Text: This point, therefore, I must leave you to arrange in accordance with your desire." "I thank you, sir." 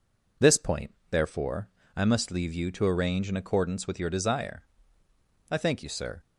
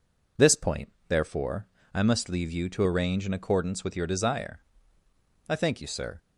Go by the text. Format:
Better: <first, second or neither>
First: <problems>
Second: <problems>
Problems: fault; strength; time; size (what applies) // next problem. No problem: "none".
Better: neither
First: none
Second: none